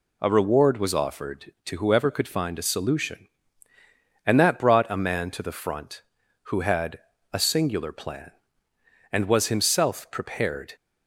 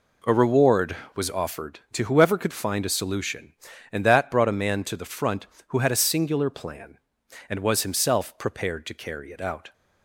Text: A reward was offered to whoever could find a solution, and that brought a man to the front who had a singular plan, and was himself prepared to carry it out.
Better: second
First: pauses between "had" and "a"; slight; at 6.9 s; 0.34 s long // stops before "to carry it out"; at 10.7 s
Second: none

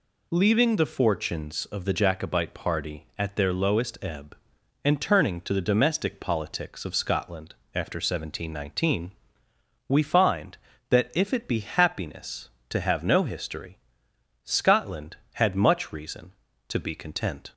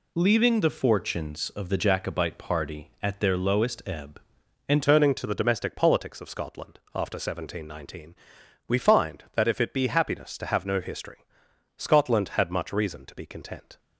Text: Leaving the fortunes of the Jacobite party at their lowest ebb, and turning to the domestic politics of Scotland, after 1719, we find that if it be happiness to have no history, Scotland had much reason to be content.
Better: first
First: none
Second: changes voice at "turning"; from 4.8 s on; 8.9 s long

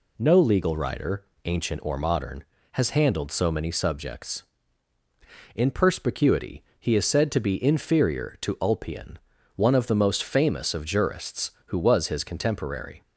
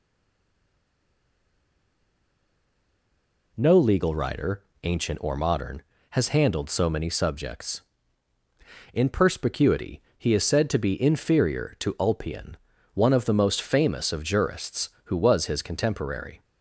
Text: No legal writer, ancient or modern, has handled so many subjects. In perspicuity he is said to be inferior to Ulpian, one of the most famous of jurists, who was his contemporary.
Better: first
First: pauses between "perspicuity" and "he"; slight; at 6.6 s; 0.16 s long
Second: stays silent before the first word; strong; until 3.5 s; 3.5 s long // pauses between "perspicuity" and "he"; slight; at 10.0 s; 0.16 s long

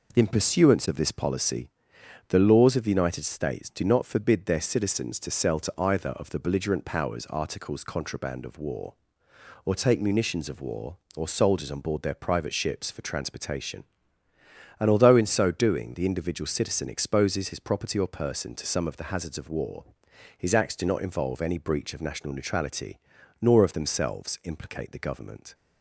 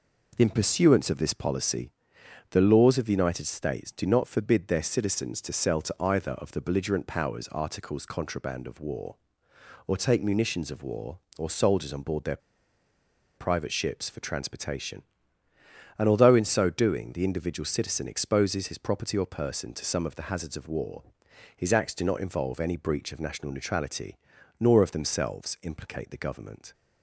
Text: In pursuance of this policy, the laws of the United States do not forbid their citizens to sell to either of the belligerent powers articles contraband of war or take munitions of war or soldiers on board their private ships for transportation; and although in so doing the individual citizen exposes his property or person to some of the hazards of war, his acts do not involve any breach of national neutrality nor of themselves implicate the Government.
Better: first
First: pauses between "neutrality" and "nor"; at 22.9 s; 0.40 s long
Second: pauses between "their" and "private"; at 12.3 s; 0.99 s long // pauses between "neutrality" and "nor"; at 24.1 s; 0.40 s long

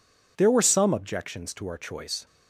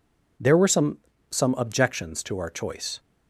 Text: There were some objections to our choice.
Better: first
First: none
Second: says "some" twice; at 1.2 s

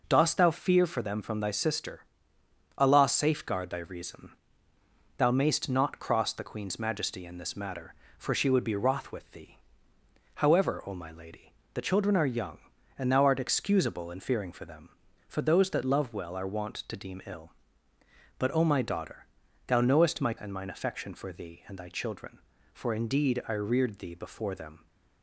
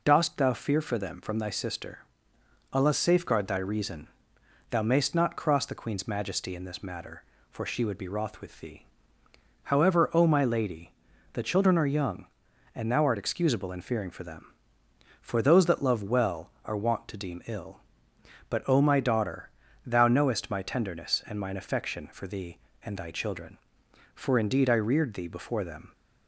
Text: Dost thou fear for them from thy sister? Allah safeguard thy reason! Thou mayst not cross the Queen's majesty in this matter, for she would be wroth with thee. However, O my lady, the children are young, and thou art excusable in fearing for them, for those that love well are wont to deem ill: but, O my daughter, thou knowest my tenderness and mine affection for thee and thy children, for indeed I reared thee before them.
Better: second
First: skips "tenderness"; at 20.3 s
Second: none

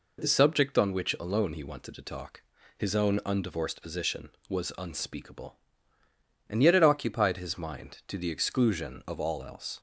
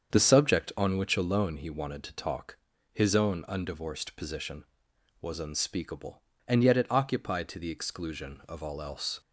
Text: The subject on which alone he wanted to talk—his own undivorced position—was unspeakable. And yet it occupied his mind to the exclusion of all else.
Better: first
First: none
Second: starts louder than the rest; strong; until 1.1 s; 7.5 dB // skips "his mind"; at 7.4 s

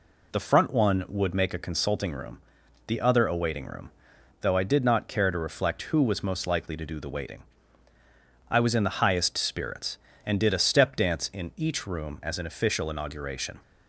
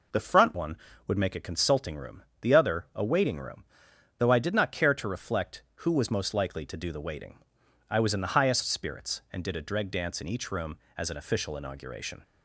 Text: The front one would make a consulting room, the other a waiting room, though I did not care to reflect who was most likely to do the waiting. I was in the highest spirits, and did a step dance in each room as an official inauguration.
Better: first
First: none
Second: says "dreg" for "step"; at 9.6 s

